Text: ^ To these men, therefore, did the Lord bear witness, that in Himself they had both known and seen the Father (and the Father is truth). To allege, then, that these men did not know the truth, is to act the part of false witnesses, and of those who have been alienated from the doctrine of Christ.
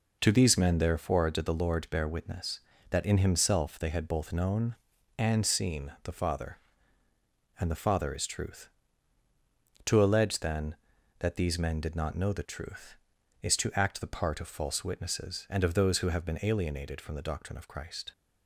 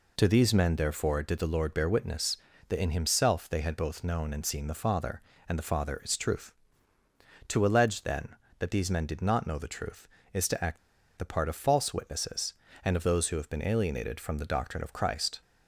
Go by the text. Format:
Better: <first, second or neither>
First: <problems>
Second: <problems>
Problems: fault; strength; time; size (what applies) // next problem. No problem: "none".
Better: first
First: none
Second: pauses between "act" and "the"; at 10.7 s; 0.40 s long